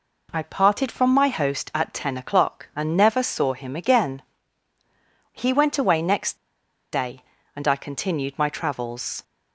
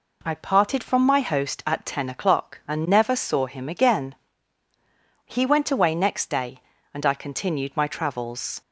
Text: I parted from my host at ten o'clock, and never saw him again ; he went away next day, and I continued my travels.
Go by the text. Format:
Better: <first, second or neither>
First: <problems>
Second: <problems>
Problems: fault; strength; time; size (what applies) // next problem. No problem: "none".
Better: second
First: pauses between "next" and "day"; noticeable; at 6.3 s; 0.56 s long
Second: none